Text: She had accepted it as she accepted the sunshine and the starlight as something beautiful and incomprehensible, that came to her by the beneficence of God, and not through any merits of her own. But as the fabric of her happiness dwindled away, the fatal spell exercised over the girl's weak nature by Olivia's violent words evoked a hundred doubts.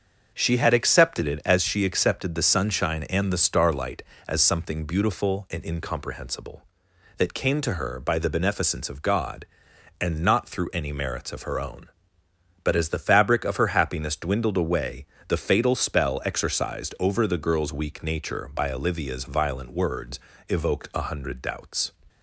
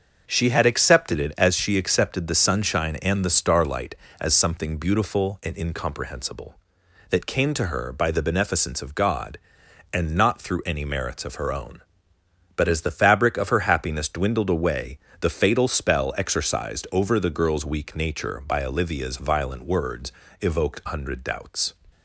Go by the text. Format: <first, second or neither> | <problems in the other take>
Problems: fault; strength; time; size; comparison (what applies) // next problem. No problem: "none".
first | starts louder than the rest; until 1.2 s; 6.5 dB; also in the first // pauses between "words" and "evoked"; slight; at 20.1 s; 0.30 s long; slight in the first // skips "a"; at 20.8 s